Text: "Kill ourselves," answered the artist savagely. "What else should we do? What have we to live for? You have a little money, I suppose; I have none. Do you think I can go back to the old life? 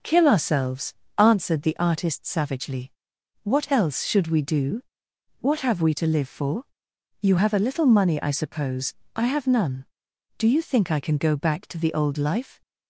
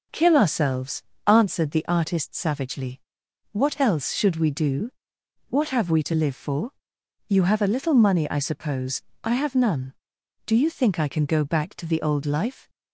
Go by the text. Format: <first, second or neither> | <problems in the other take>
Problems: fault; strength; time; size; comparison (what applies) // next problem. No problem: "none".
neither | none